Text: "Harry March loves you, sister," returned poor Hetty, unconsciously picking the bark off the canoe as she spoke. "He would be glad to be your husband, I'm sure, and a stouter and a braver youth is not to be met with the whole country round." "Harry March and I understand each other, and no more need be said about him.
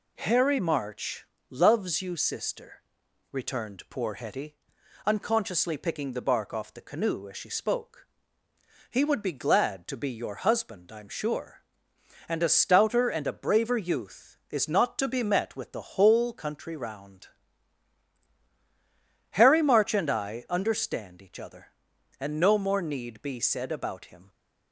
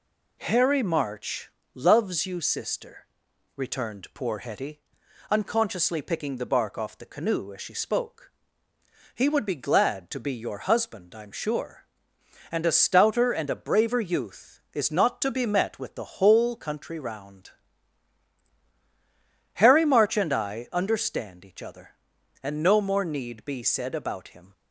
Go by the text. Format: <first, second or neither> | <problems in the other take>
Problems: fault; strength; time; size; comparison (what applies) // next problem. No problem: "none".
neither | pauses between "March" and "loves"; slight; the same in both